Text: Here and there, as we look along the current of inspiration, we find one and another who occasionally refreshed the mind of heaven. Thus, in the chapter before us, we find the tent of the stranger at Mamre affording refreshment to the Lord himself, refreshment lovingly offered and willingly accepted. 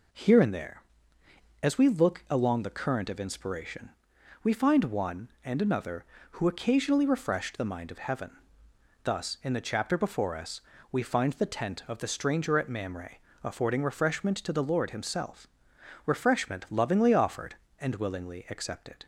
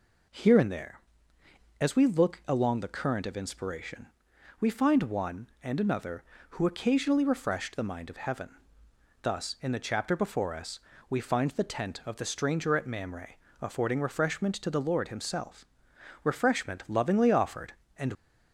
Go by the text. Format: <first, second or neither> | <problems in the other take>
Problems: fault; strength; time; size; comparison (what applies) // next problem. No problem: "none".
first | pauses between "Mamre" and "affording"; slight; at 13.3 s; 0.26 s long; slight in the first // stops before "willingly accepted"; at 18.1 s